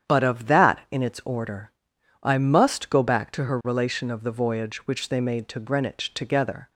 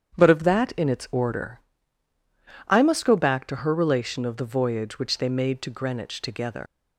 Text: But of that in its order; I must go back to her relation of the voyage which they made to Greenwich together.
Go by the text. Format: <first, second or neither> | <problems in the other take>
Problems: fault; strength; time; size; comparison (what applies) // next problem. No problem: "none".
first | starts louder than the rest; strong; until 1.1 s; 8.5 dB; strong in the first // leaves "together" unfinished; at 6.6 s; 155 ms